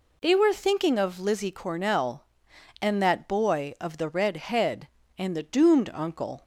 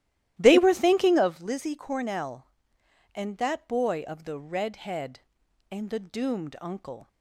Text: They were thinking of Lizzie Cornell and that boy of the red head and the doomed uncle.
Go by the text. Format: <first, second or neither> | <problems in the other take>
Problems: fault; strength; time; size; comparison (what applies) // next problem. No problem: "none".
first | starts louder than the rest; strong; until 1.4 s; 14 dB